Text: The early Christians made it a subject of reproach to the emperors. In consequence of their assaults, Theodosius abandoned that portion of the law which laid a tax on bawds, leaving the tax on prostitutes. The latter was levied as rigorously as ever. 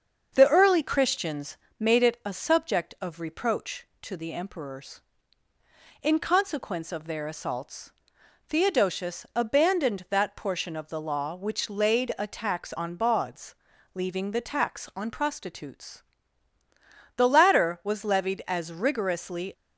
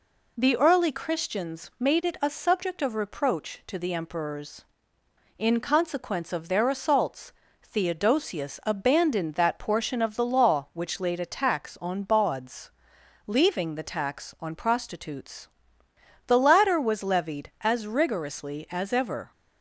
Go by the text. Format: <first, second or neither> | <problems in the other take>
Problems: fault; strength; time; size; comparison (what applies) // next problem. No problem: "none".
second | starts louder than the rest; until 1.3 s; 6.5 dB // pauses between "Christians" and "made"; slight; at 1.5 s; 0.20 s long // stops before "as ever"; at 19.5 s